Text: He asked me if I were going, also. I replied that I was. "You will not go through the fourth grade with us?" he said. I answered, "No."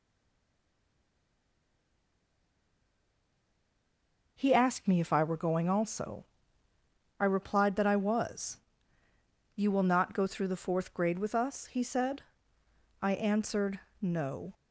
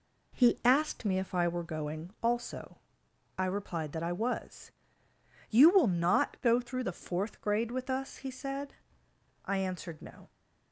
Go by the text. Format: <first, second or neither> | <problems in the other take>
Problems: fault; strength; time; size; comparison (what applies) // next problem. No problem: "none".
second | stays silent before the first word; strong; until 4.3 s; 4.3 s long